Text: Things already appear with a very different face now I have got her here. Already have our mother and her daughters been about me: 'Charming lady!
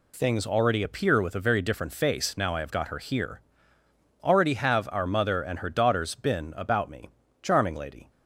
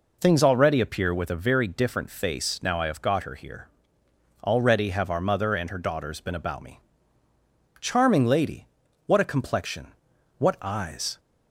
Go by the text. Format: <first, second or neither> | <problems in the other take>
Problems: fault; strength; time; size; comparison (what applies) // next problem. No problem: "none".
first | goes on to say "What a complexion What eyes"; strong; from 9.0 s on; 2.1 s long